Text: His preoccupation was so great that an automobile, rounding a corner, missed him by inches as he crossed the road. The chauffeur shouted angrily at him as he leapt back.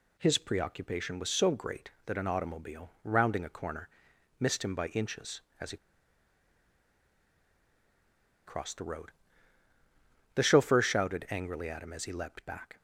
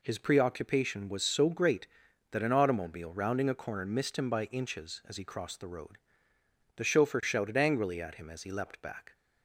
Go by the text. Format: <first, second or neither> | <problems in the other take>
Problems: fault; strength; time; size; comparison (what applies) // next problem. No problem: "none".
second | pauses between "he" and "crossed"; strong; at 5.7 s; 2.6 s long